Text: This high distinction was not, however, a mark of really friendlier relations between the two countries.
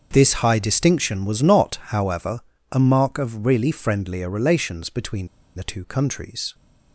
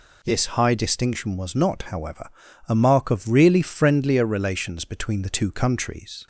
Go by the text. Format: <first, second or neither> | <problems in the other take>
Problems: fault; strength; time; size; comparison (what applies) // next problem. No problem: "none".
second | starts louder than the rest; until 1.1 s; 6.5 dB // pauses between "between" and "the"; slight; at 5.2 s; 0.28 s long